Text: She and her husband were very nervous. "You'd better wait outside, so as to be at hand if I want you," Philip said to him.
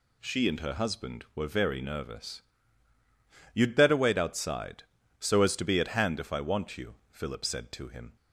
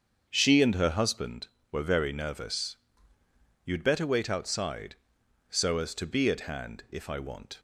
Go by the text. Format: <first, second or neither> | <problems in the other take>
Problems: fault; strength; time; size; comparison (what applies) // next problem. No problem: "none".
first | starts louder than the rest; until 1.3 s; 7 dB // stops before "you Philip said to him"; at 7.5 s